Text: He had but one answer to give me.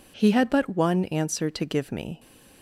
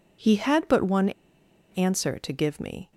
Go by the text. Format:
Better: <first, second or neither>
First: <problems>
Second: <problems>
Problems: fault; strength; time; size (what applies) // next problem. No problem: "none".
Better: first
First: none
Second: pauses between "one" and "answer"; noticeable; at 1.1 s; 0.59 s long